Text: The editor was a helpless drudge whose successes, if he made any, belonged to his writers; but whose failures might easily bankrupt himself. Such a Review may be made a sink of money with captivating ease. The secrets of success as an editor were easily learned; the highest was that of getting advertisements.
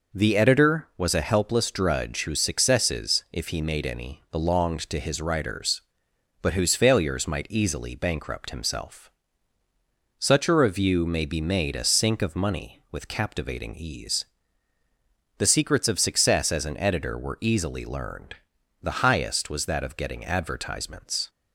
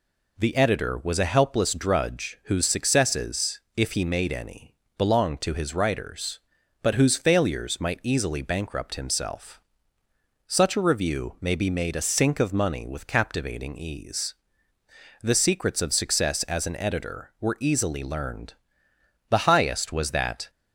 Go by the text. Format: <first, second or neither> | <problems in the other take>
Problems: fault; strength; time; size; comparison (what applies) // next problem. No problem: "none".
first | stops before "of getting advertisements"; at 20.4 s